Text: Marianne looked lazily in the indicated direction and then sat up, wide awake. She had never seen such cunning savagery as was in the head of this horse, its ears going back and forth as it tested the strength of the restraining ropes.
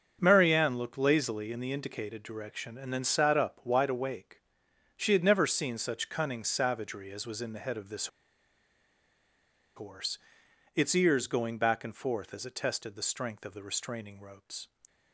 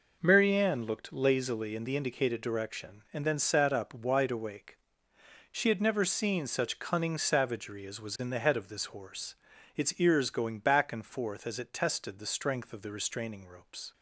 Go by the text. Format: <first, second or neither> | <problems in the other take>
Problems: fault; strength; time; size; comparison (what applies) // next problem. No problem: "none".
second | starts louder than the rest; until 1.2 s; 6.5 dB // pauses between "this" and "horse"; strong; at 8.0 s; 1.6 s long